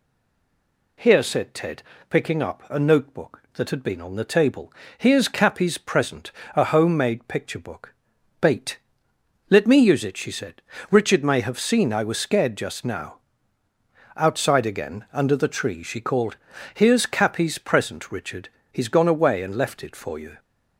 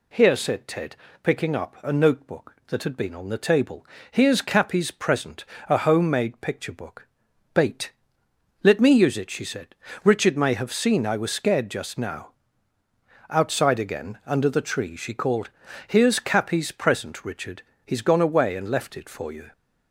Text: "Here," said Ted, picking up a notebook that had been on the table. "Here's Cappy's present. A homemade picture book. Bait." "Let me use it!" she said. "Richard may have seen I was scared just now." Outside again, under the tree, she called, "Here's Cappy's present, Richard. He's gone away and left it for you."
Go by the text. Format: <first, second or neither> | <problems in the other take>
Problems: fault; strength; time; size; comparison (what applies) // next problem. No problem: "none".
second | stays silent before the first word; until 0.9 s; 0.9 s long